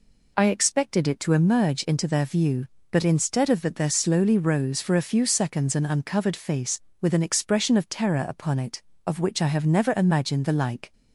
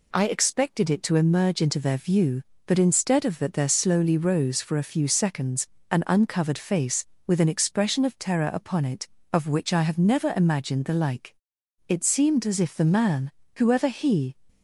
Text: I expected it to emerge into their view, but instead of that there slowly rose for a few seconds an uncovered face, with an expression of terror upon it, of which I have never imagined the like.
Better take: first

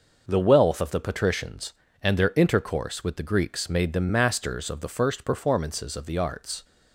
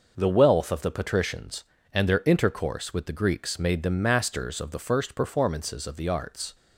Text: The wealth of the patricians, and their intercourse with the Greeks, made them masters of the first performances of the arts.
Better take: neither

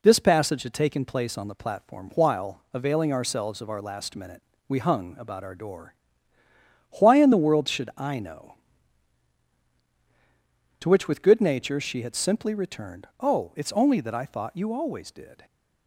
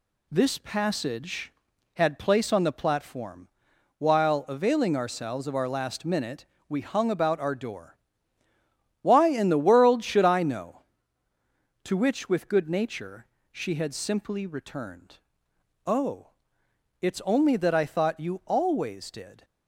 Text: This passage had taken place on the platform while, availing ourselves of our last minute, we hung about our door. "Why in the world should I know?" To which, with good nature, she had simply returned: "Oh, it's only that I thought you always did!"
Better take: first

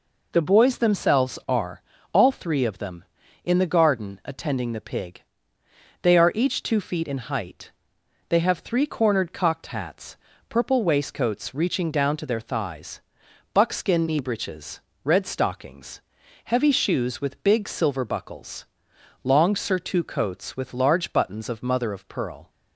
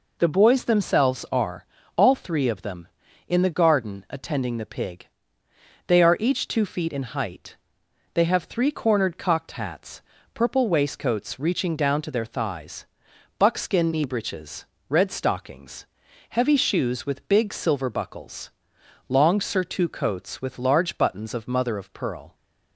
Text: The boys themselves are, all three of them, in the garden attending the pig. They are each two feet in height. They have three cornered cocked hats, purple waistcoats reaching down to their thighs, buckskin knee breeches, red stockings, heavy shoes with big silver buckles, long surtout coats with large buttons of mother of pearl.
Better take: neither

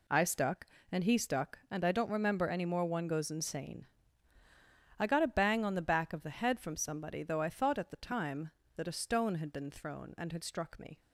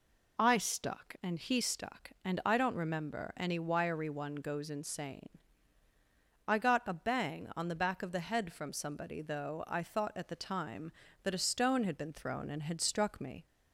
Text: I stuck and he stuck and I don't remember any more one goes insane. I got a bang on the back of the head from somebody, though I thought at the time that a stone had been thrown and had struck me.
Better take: first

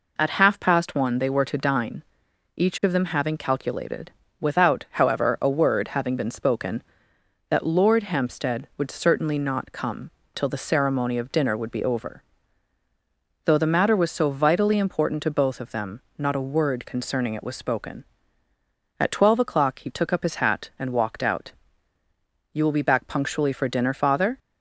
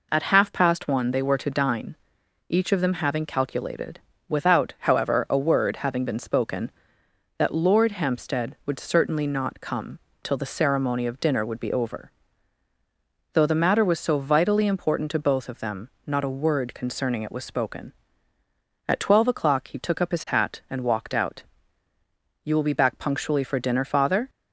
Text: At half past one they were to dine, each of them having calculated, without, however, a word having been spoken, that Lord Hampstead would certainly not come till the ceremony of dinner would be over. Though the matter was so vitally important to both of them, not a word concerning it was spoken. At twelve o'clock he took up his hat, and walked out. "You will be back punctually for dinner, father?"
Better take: neither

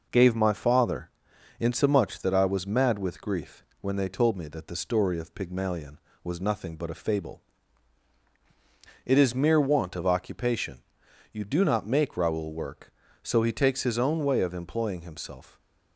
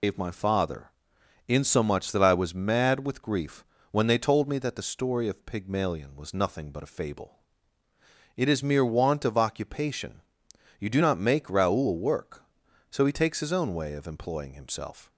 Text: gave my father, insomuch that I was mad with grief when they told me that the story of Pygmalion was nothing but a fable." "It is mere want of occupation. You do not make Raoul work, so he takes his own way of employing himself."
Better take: first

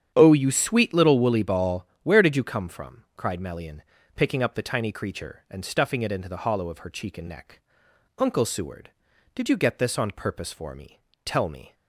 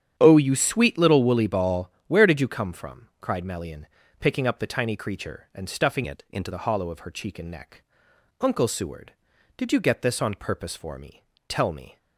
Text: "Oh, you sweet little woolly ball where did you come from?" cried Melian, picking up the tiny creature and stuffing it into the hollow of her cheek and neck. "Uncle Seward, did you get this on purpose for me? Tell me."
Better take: first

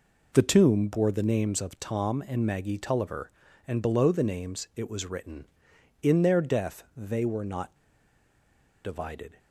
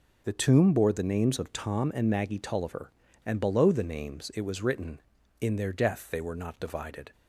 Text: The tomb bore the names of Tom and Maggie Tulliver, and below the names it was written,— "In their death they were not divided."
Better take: second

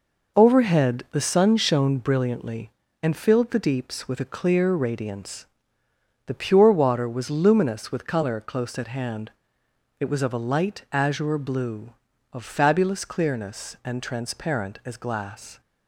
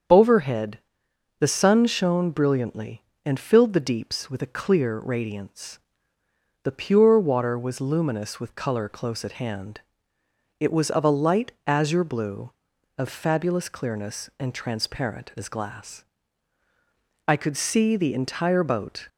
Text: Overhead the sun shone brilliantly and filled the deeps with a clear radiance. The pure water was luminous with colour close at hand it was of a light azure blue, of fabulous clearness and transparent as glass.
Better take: first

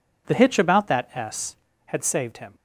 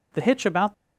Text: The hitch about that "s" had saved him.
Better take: first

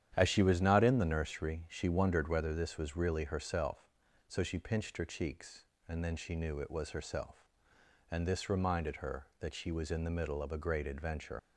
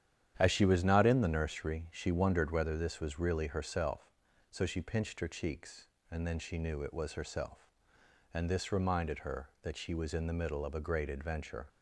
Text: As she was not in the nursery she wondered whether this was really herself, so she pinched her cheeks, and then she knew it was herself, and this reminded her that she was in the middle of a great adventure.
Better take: second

